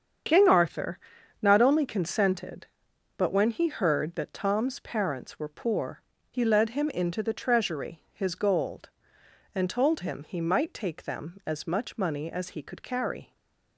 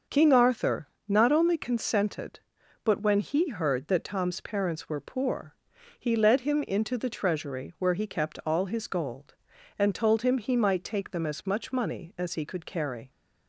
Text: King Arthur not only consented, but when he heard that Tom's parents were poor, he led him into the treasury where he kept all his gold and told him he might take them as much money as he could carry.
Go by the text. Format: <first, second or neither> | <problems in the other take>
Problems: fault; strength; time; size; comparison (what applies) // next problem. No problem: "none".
second | starts louder than the rest; strong; until 1.7 s; 7.5 dB; also in the second // pauses between "Arthur" and "not"; at 0.9 s; 0.42 s long; slight in the second // skips "where he kept all"; at 8.0 s // stays silent after the last word; slight; from 13.2 s on; 0.5 s long